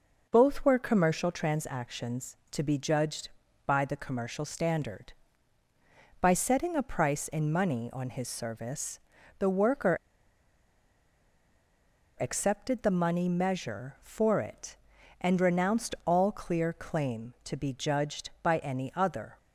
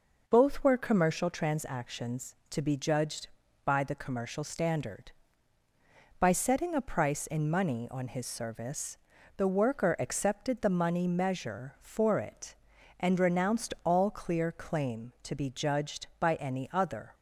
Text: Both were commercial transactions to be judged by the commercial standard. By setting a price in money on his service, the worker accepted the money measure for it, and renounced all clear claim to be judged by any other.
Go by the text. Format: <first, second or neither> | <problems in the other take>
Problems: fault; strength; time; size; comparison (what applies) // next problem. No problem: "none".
second | pauses between "worker" and "accepted"; strong; at 9.9 s; 2.2 s long